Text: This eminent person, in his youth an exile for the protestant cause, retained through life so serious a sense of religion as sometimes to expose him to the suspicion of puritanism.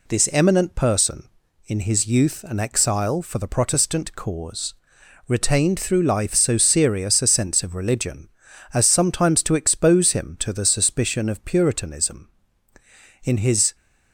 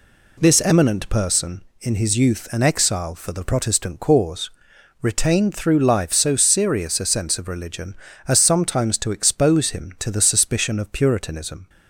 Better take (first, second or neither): second